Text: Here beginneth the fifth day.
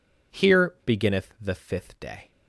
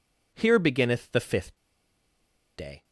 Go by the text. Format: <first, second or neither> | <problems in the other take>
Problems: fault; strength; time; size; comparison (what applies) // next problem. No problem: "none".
first | pauses between "fifth" and "day"; at 1.5 s; 0.99 s long